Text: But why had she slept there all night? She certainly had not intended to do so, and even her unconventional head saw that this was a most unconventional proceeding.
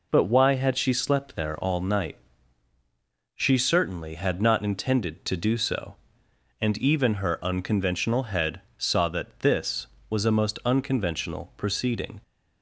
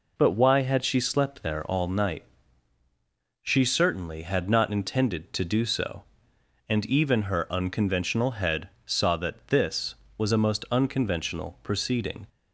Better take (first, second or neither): neither